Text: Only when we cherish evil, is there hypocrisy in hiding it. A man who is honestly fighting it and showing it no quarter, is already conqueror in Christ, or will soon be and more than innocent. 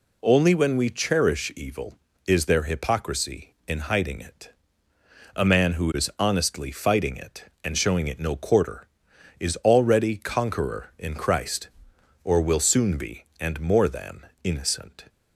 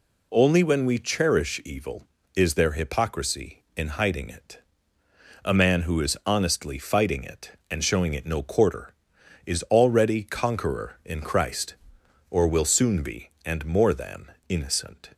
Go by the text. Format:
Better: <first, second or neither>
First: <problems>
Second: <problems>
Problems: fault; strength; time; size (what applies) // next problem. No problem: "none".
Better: neither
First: pauses between "than" and "innocent"; slight; at 14.2 s; 0.18 s long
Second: pauses between "than" and "innocent"; slight; at 14.3 s; 0.18 s long